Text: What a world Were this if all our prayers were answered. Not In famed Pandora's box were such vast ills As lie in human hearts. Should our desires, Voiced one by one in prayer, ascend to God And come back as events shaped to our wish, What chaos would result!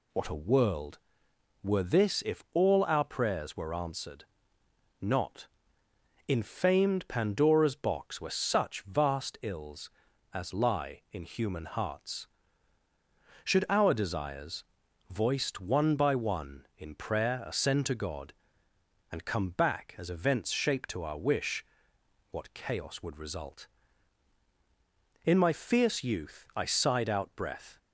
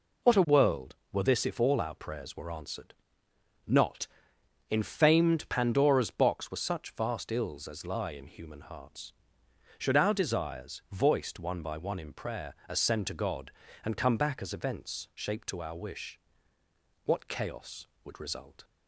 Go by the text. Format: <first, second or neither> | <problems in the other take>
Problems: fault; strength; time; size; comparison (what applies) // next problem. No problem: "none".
second | goes on to say "In my fierce youth I sighed out breath"; strong; from 25.2 s on; 2.5 s long